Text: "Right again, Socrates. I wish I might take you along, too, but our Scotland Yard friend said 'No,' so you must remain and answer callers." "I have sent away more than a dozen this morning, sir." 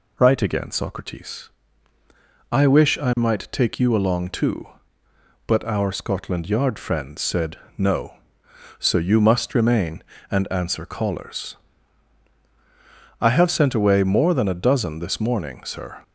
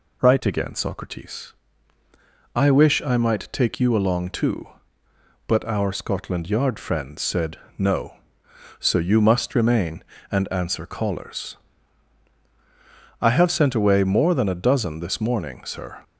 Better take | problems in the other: neither | pauses between "said" and "No"; slight; the same in both

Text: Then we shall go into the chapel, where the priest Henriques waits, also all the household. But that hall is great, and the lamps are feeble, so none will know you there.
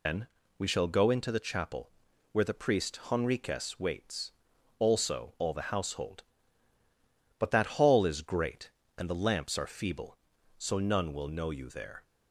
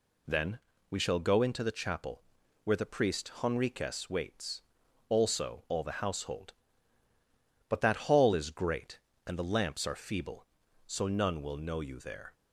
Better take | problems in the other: second | loses the start of "Then"; at 0.0 s; 100 ms // pauses between "Then" and "we"; slight; at 0.2 s; 0.30 s long; slight in the second

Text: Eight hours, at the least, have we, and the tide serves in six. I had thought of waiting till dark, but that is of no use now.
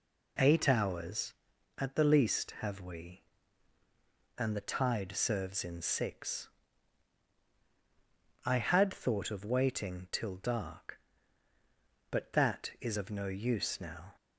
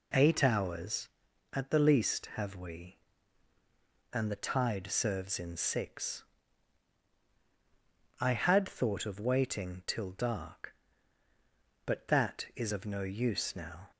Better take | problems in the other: neither | none

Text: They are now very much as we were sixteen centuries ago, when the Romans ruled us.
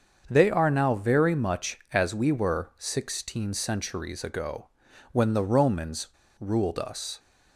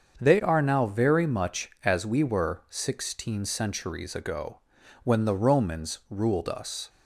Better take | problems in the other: second | starts louder than the rest; until 1.2 s; 7 dB; also in the second // pauses between "Romans" and "ruled"; slight; at 6.0 s; 0.31 s long

